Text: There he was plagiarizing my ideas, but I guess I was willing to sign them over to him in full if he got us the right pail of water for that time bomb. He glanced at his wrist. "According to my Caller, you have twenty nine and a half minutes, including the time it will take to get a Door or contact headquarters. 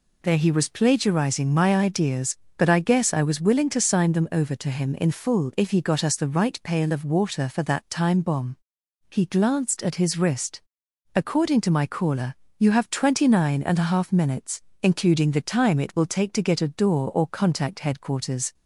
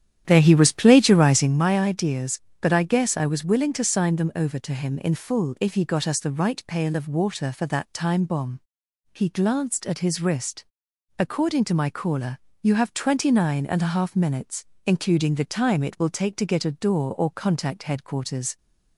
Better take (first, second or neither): first